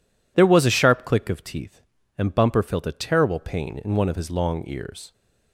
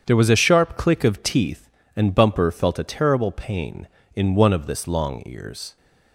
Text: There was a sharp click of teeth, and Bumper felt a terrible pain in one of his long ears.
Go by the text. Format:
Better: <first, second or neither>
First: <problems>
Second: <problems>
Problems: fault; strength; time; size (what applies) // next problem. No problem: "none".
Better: first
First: none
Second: starts louder than the rest; strong; until 1.0 s; 8 dB // says "this" for "his"; at 4.6 s